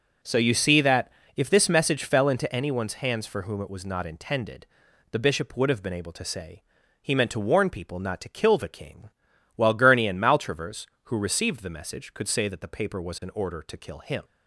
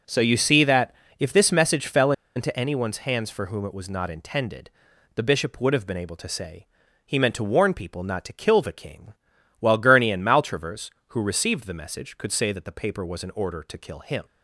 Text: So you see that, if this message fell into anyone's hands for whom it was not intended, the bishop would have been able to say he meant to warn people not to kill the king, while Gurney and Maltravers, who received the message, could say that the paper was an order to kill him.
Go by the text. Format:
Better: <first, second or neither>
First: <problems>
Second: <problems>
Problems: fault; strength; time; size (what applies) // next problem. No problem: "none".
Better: first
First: pauses between "say" and "he"; at 6.6 s; 0.40 s long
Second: pauses between "fell" and "into"; slight; at 2.1 s; 0.24 s long // pauses between "say" and "he"; at 6.6 s; 0.40 s long